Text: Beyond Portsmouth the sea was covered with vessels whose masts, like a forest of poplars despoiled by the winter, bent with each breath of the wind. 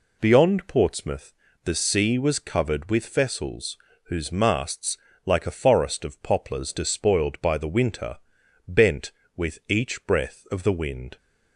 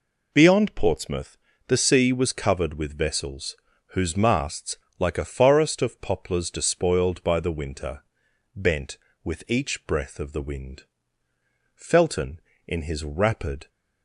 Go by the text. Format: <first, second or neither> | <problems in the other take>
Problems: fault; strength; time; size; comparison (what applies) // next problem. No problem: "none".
first | pauses between "Portsmouth" and "the"; slight; at 1.3 s; 0.30 s long; slight in the first // pauses between "vessels" and "whose"; slight; at 3.5 s; 0.36 s long; slight in the first // goes on to say "Felton in his rapid"; strong; from 11.7 s on; 1.9 s long